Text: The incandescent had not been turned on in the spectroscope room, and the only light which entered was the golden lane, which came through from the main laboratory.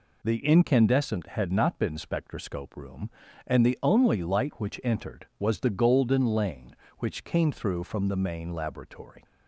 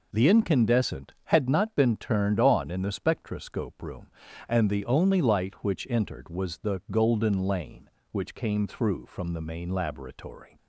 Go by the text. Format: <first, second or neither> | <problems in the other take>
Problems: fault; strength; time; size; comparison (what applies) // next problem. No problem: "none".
second | skips "turned on in the"; at 1.9 s